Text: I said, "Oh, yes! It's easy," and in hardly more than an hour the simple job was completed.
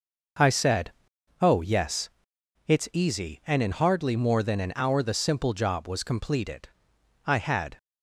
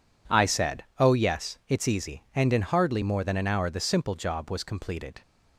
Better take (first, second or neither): second